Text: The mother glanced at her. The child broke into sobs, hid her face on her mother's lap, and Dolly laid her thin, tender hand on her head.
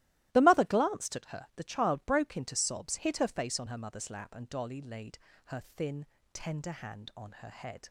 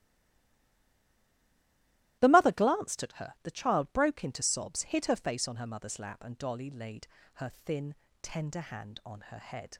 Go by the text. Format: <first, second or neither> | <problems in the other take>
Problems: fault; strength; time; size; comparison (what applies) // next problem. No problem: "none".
first | stays silent before the first word; until 2.1 s; 2.1 s long // starts louder than the rest; strong; until 3.2 s; 16 dB; strong in the first // pauses between "laid" and "her"; slight; at 7.0 s; 0.28 s long; slight in the first